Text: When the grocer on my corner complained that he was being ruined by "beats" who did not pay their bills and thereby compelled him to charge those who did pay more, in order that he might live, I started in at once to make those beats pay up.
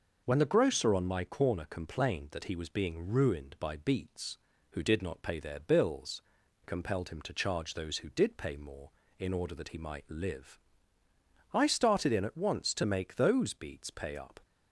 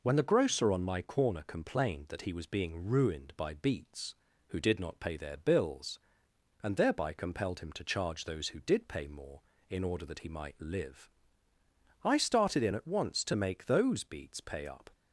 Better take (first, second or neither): second